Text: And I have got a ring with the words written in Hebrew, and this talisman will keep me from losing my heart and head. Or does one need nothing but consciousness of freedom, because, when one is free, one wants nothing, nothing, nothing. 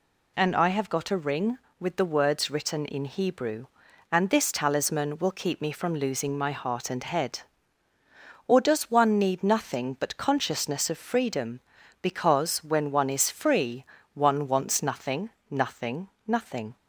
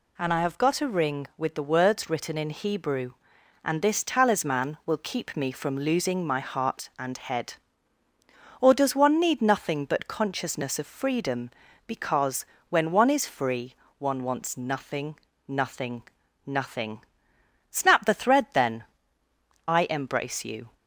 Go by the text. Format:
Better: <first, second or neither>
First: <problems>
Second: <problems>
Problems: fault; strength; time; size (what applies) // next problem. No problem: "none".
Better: first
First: none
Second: goes on to say "Snap the thread then I embrace you"; strong; from 17.7 s on; 3.0 s long